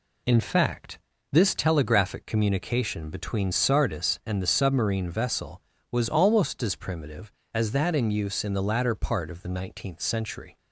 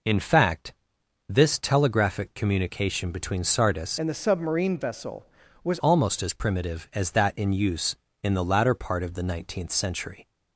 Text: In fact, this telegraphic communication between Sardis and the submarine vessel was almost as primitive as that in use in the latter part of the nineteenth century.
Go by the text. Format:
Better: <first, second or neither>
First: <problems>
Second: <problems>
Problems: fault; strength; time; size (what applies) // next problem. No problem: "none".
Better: first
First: none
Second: changes voice from "and" to "was"; from 3.9 to 5.7 s; 1.8 s long